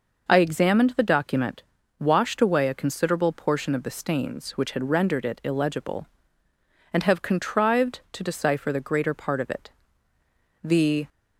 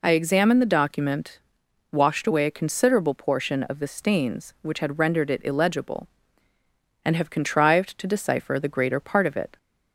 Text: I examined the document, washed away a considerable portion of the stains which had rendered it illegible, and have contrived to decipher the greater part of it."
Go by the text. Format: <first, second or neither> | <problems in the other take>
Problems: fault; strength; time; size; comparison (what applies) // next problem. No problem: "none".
second | goes on to say "The"; slight; from 10.6 s on; 0.46 s long